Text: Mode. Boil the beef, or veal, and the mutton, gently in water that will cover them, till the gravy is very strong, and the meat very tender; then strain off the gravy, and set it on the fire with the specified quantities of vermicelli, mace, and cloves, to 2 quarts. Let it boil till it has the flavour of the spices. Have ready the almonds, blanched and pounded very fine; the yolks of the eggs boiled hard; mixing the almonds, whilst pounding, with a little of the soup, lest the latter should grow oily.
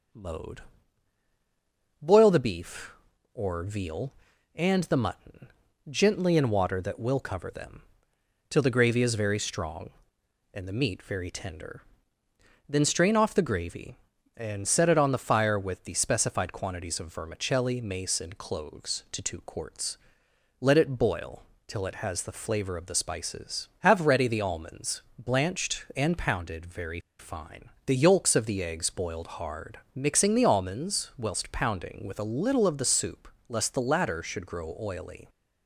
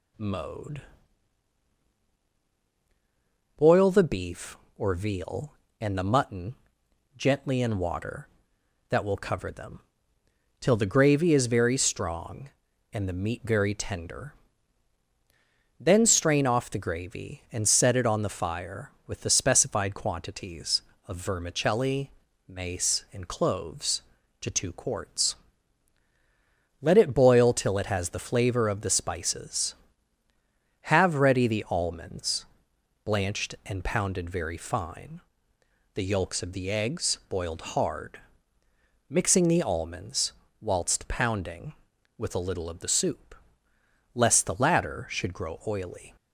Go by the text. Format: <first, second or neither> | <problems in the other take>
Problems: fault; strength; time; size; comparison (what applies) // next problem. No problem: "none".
second | starts louder than the rest; noticeable; until 2.5 s; 6 dB // pauses between "boil" and "till"; slight; at 21.4 s; 0.24 s long // pauses between "very" and "fine"; slight; at 26.9 s; 0.20 s long